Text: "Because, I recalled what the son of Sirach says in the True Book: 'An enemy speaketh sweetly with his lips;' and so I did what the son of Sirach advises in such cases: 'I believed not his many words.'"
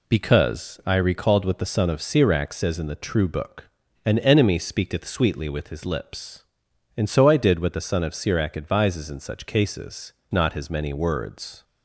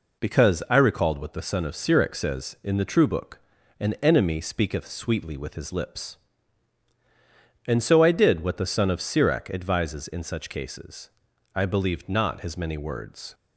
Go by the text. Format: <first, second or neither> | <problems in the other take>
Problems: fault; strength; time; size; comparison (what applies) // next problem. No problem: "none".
second | skips "I believed"; at 10.2 s